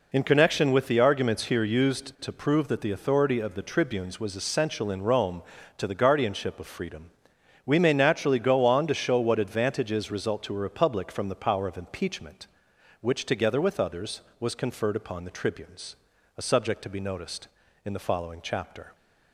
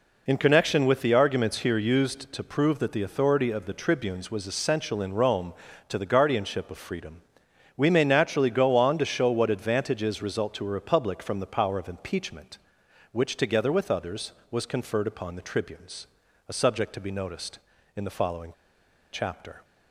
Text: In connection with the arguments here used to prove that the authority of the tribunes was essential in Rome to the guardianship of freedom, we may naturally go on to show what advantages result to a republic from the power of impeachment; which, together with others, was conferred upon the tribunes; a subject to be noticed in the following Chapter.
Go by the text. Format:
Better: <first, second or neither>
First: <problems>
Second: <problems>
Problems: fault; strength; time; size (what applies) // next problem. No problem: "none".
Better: first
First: none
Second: pauses between "following" and "Chapter"; noticeable; at 18.4 s; 0.62 s long